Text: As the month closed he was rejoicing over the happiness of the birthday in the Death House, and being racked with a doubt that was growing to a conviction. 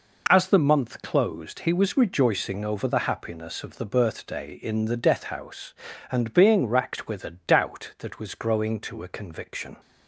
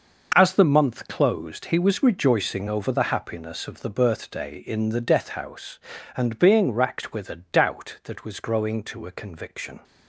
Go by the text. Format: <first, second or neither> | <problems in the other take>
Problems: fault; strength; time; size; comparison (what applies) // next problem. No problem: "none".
first | gets quieter; strong; throughout; 10.5 dB